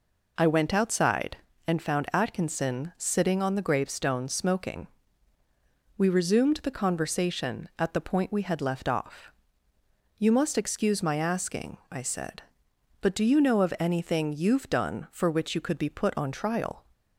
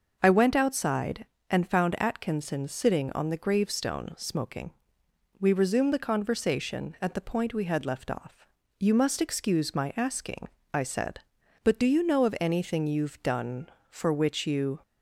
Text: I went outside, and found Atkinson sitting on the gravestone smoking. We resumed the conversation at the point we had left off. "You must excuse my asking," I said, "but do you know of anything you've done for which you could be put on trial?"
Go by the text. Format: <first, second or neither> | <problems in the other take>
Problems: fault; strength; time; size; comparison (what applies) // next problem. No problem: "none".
first | starts louder than the rest; until 1.2 s; 6 dB // stops before "could be put on trial"; at 14.8 s